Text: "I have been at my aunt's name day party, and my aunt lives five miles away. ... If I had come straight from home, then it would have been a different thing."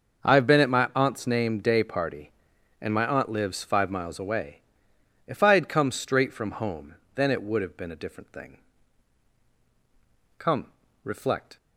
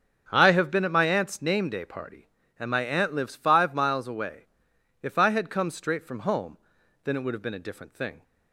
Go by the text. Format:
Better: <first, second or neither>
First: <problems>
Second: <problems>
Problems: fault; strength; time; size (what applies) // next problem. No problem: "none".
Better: second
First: starts louder than the rest; noticeable; until 1.2 s; 6 dB // goes on to say "Come reflect"; noticeable; from 10.3 s on; 1.2 s long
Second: starts louder than the rest; strong; until 1.3 s; 7.5 dB